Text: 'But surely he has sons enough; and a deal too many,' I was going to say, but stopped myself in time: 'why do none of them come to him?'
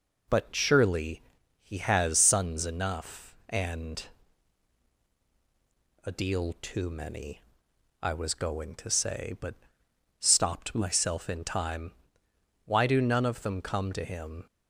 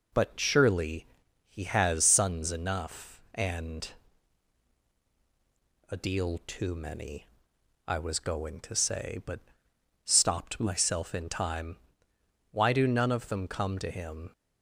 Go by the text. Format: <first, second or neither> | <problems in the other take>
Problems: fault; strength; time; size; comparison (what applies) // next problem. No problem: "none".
neither | pauses between "surely" and "he"; the same in both // pauses between "and" and "a"; strong; the same in both // pauses between "but" and "stopped"; noticeable; the same in both